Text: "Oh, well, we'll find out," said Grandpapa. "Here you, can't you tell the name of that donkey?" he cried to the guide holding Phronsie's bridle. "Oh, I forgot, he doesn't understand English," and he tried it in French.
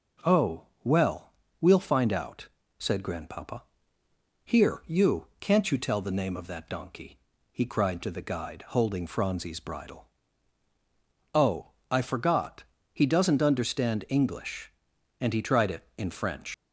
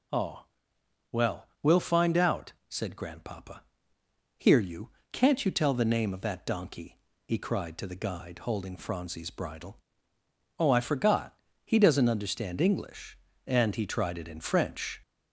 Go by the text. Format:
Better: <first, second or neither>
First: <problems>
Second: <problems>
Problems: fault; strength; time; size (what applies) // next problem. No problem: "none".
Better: second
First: leaves "French" unfinished; at 16.5 s; 115 ms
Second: none